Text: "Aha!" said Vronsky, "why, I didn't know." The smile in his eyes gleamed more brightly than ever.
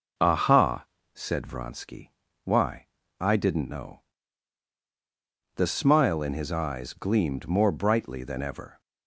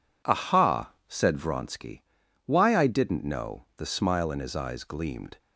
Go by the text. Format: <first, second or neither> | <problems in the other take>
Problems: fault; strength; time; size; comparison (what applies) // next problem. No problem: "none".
first | stops before "more brightly than ever"; at 5.3 s